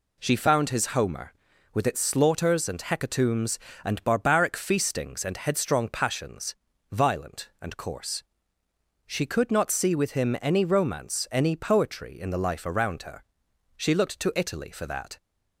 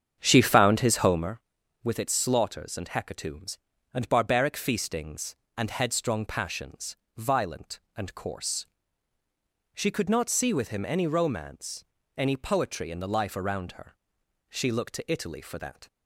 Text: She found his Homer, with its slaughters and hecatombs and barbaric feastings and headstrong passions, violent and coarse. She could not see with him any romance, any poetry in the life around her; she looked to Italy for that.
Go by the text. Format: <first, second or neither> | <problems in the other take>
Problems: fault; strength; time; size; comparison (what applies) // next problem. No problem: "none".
first | starts louder than the rest; strong; until 1.4 s; 8 dB